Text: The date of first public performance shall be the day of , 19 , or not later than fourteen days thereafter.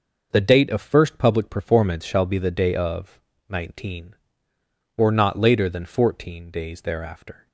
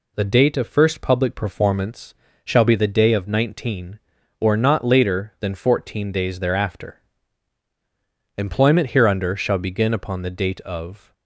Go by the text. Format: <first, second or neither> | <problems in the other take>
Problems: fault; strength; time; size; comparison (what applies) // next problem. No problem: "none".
first | pauses between "performance" and "shall"; slight; at 2.1 s; 0.30 s long // goes on to say "Employment hereunder shall begin upon the date of"; strong; from 8.3 s on; 2.7 s long